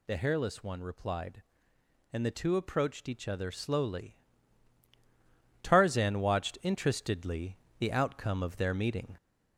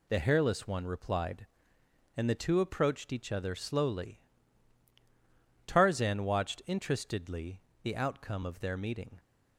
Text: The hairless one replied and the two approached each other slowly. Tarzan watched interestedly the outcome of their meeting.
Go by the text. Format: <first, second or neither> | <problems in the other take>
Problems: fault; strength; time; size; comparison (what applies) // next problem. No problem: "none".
second | gets louder; slight; throughout; 2.5 dB // pauses between "interestedly" and "the"; slight; at 7.5 s; 0.22 s long; slight in the second